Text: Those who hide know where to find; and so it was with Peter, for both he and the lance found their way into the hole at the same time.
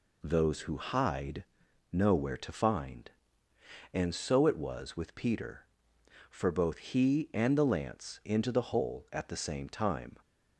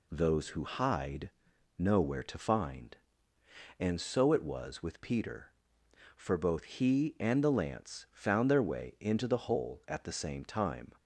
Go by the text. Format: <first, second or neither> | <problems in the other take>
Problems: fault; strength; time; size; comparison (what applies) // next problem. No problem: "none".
second | pauses between "hide" and "know"; noticeable; at 1.4 s; 0.46 s long; noticeable in the second // skips "found their way"; at 8.2 s